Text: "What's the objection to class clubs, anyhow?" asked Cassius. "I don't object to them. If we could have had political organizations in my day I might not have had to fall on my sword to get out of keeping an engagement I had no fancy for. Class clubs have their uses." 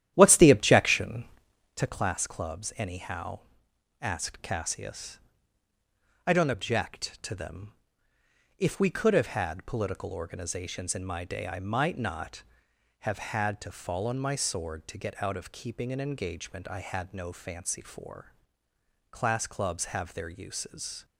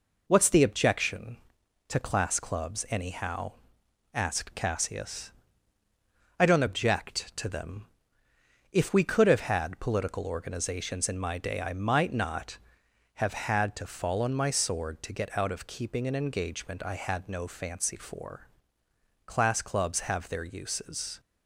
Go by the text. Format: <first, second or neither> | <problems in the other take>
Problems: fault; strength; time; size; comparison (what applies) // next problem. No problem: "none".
second | starts louder than the rest; strong; until 1.9 s; 12 dB